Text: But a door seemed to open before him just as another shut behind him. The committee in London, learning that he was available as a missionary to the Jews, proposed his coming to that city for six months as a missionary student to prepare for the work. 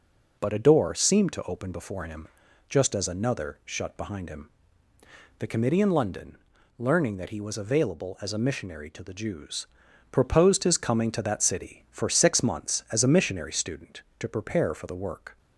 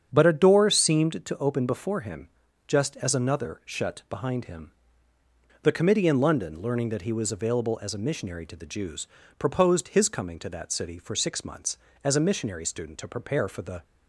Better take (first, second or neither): first